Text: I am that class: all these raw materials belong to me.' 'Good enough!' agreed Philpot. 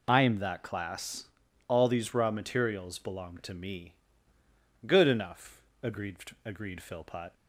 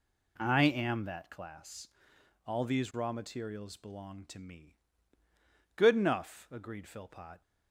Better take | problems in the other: second | says "agreed" twice; at 6.4 s

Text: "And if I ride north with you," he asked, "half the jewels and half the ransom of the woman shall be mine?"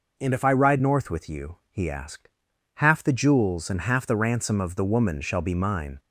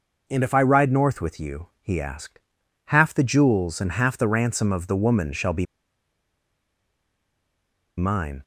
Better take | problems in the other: first | pauses between "be" and "mine"; strong; at 5.6 s; 2.3 s long

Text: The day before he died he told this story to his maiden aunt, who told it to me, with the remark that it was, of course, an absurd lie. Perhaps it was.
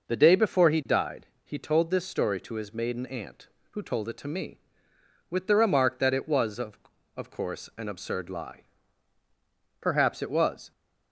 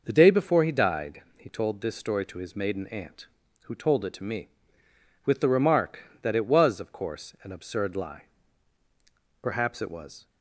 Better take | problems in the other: second | pauses between "died" and "he"; slight; at 1.2 s; 0.18 s long; slight in the second // says "of" twice; at 7.1 s

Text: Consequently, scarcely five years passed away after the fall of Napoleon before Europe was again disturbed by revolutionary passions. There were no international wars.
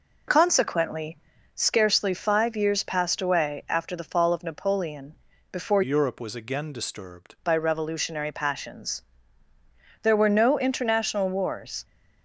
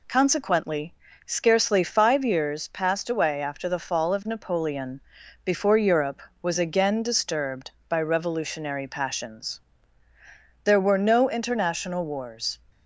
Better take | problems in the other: second | pauses between "Napoleon" and "before"; slight; at 5.1 s; 0.36 s long; also in the second // changes voice from "Europe" to "disturbed"; from 5.8 to 7.3 s; 1.5 s long

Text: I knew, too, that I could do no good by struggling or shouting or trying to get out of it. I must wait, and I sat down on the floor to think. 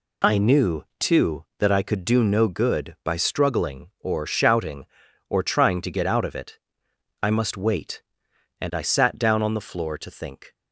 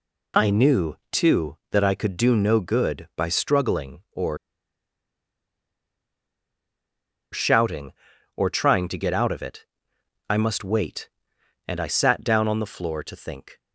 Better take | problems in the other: first | pauses between "or" and "shouting"; strong; at 4.3 s; 2.9 s long

